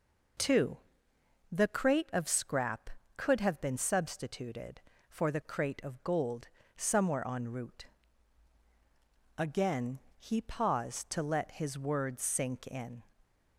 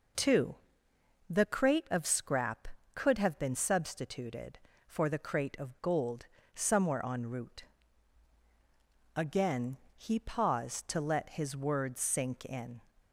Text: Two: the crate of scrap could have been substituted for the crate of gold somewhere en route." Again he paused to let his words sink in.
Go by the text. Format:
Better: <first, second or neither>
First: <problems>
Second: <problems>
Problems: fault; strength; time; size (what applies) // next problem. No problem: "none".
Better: neither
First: pauses between "gold" and "somewhere"; slight; at 6.4 s; 0.28 s long // pauses between "Again" and "he"; slight; at 9.9 s; 0.18 s long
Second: pauses between "gold" and "somewhere"; slight; at 6.2 s; 0.28 s long // pauses between "Again" and "he"; slight; at 9.7 s; 0.18 s long